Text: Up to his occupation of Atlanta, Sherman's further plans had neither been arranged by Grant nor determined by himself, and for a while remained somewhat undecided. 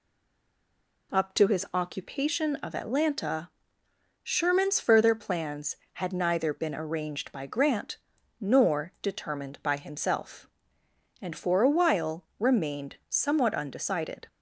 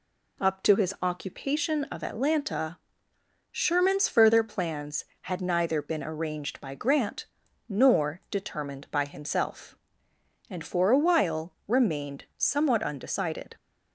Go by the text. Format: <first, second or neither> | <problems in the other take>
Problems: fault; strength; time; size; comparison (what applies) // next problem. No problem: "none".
second | stays silent before the first word; until 1.1 s; 1.1 s long // pauses between "Grant" and "nor"; at 7.9 s; 0.42 s long; also in the second